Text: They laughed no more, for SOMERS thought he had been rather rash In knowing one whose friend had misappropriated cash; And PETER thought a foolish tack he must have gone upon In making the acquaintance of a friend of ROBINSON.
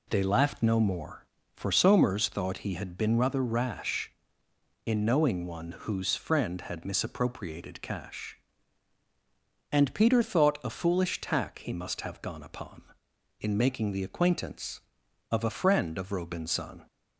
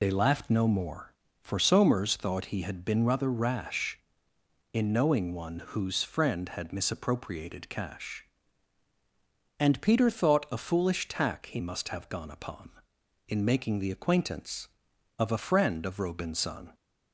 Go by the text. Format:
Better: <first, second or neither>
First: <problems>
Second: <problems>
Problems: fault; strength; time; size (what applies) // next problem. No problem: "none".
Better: first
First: none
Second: loses the start of "They"; at 0.0 s; 65 ms